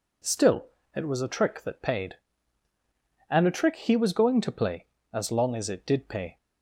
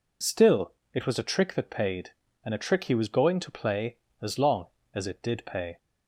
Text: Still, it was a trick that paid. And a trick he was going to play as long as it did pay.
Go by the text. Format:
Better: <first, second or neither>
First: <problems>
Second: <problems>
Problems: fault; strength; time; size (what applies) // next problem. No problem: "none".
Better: neither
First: none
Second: none